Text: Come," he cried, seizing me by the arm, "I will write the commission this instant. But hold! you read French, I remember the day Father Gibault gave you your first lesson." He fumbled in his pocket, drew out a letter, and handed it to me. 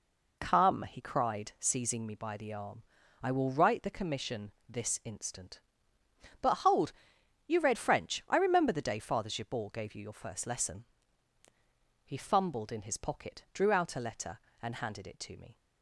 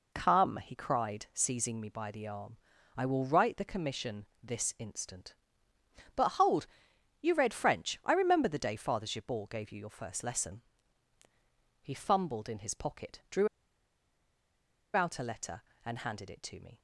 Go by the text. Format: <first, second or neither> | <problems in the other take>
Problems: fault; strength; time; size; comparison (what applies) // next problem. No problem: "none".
first | pauses between "commission" and "this"; slight; at 4.2 s; 0.16 s long; slight in the first // pauses between "drew" and "out"; strong; at 13.4 s; 1.4 s long